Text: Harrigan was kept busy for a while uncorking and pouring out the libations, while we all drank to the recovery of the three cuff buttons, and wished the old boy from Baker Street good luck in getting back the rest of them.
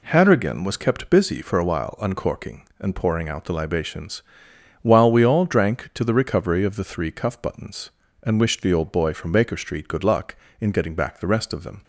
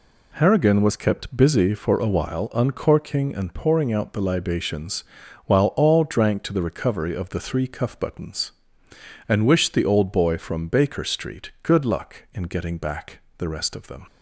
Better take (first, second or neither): first